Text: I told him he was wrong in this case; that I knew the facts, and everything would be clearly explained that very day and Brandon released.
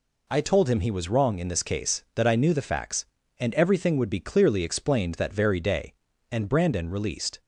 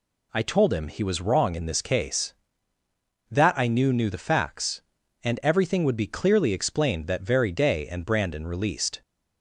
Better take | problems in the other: first | says "knew" twice; at 3.9 s

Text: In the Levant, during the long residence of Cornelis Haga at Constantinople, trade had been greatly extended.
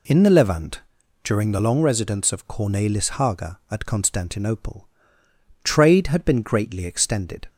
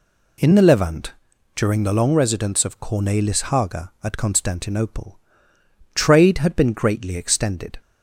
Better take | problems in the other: neither | none

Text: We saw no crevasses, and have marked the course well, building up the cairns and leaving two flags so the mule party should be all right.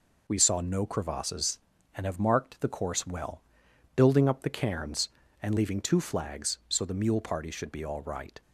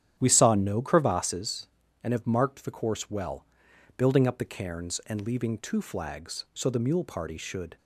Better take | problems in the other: first | starts louder than the rest; strong; until 1.2 s; 10 dB // stops before "be all right"; at 7.7 s

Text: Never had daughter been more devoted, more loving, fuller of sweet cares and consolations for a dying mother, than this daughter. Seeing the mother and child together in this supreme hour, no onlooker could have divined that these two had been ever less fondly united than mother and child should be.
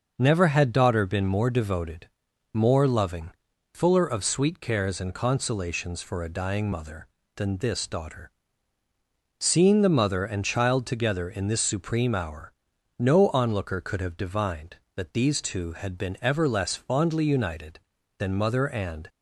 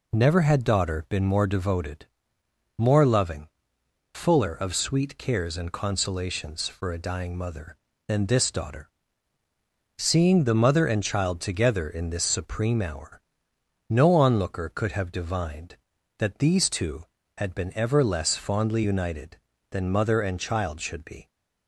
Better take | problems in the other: second | starts louder than the rest; noticeable; until 1.1 s; 6 dB // stops before "child should be"; at 19.0 s

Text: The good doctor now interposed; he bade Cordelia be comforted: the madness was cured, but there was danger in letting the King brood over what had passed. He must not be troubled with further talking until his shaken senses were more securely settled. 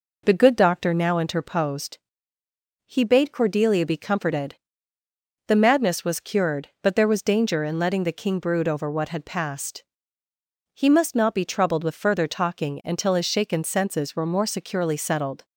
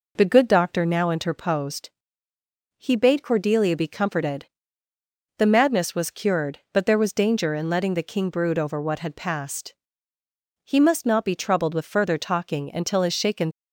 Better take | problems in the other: first | stops before "senses were more securely settled"; at 13.5 s

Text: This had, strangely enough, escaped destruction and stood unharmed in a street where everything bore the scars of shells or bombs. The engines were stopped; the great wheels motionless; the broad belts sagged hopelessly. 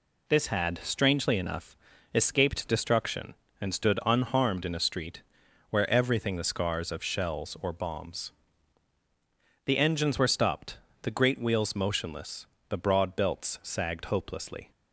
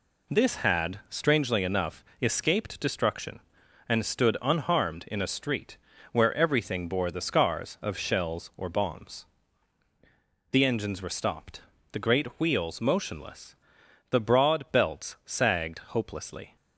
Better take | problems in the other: second | pauses between "street" and "where"; noticeable; at 5.2 s; 0.48 s long; slight in the second // skips "bore"; at 6.3 s

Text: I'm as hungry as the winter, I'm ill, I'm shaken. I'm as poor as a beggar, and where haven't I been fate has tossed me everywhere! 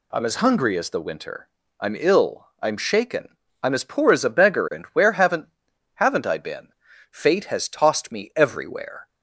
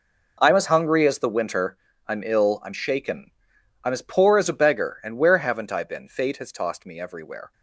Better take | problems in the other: second | says "haven't" twice; at 5.9 s // pauses between "been" and "fate"; at 6.6 s; 0.42 s long

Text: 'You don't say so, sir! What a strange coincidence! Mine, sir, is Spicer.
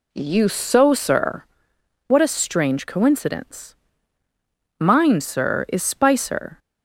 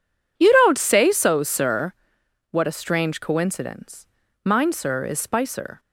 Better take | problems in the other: second | skips "don't say"; at 0.4 s

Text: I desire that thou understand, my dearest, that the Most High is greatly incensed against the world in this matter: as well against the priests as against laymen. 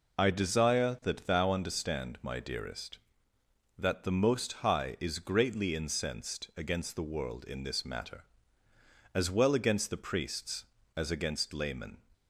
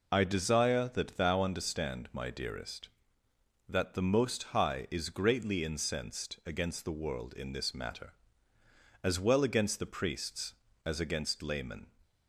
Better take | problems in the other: neither | none

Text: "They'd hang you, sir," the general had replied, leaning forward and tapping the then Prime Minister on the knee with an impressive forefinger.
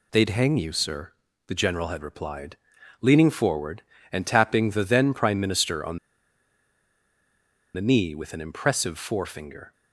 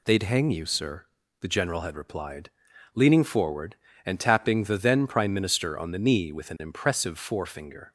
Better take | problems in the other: second | pauses between "on" and "the"; strong; at 5.9 s; 1.7 s long

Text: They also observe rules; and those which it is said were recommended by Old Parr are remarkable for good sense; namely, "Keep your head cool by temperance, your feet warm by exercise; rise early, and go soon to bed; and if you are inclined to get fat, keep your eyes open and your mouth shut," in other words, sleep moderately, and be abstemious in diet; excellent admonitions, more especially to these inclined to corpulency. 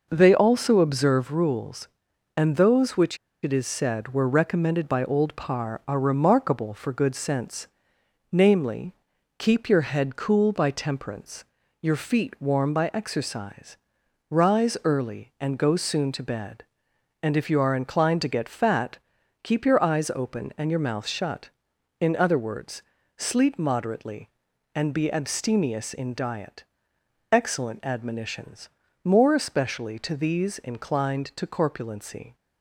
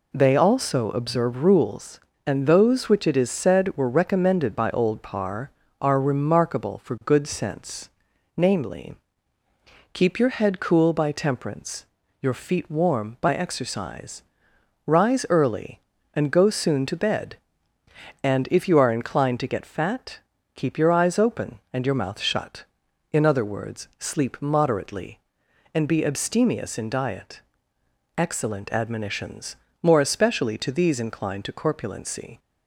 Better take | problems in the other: second | pauses between "which" and "it"; slight; at 3.1 s; 0.27 s long

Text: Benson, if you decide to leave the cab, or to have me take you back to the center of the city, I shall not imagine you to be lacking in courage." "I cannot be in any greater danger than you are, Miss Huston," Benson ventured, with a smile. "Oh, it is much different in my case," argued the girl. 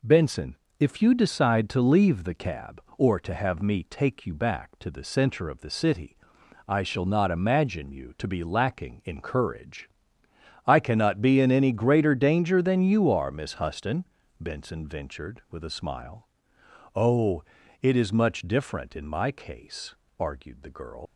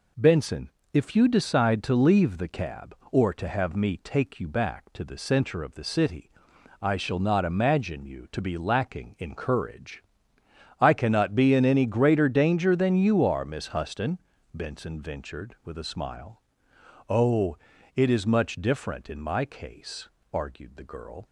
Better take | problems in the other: second | leaves "girl" unfinished; at 21.0 s; 70 ms

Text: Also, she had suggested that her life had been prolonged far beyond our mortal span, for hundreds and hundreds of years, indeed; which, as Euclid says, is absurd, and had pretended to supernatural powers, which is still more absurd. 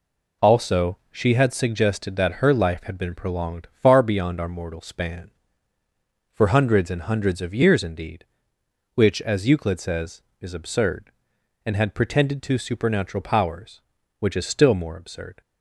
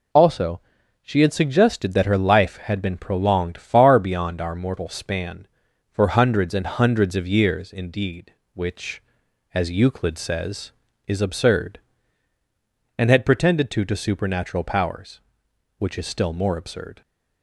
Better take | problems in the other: first | says "to" twice; at 13.8 s

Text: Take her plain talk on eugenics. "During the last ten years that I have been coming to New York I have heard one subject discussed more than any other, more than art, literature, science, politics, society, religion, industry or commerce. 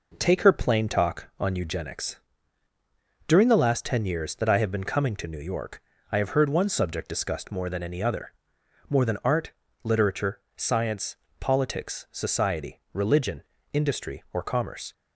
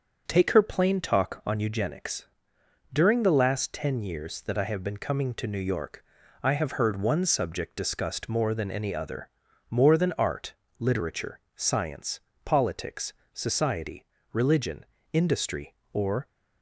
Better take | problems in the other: first | starts louder than the rest; until 1.2 s; 6.5 dB // pauses between "York" and "I"; at 6.0 s; 0.40 s long; slight in the first // stops before "commerce"; at 16.2 s

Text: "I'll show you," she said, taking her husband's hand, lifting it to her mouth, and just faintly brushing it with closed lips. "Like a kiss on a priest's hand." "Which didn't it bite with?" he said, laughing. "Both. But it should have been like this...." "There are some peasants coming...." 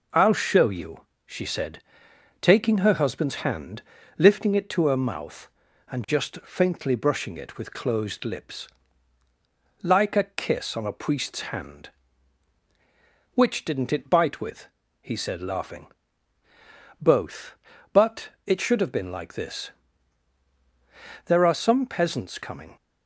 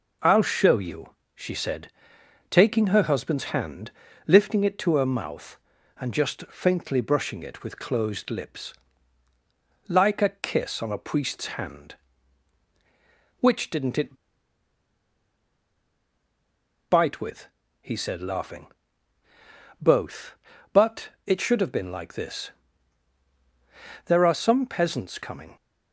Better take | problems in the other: first | pauses between "it" and "bite"; strong; at 14.1 s; 2.7 s long // pauses between "But" and "it"; slight; at 21.0 s; 0.16 s long; slight in the first

